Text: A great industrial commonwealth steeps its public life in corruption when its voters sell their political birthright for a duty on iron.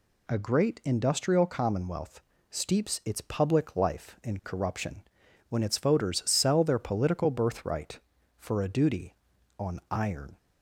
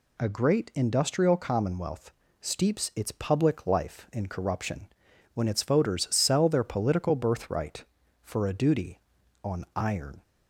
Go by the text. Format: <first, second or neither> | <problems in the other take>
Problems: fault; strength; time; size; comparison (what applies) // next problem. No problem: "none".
neither | pauses between "commonwealth" and "steeps"; slight; the same in both // pauses between "corruption" and "when"; noticeable; the same in both